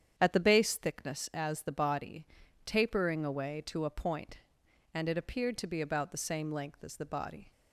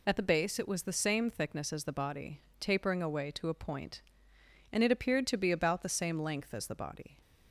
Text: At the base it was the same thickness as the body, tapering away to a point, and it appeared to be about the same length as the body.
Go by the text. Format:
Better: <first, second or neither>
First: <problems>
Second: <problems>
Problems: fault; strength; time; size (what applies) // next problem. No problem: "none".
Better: second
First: starts louder than the rest; strong; until 1.2 s; 8.5 dB // skips "it was the same"; at 0.7 s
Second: none